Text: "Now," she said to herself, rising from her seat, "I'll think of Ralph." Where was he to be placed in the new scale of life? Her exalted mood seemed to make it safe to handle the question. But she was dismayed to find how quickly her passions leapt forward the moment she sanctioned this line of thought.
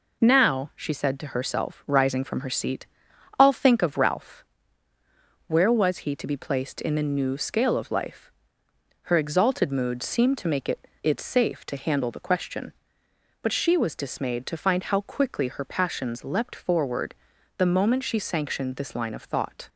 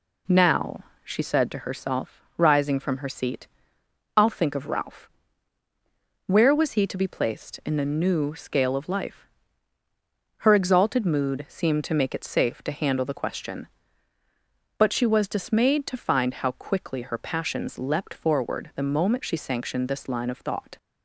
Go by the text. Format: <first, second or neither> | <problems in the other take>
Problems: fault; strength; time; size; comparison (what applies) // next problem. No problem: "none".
second | says "it" twice; at 11.0 s // pauses between "forward" and "the"; at 17.1 s; 0.42 s long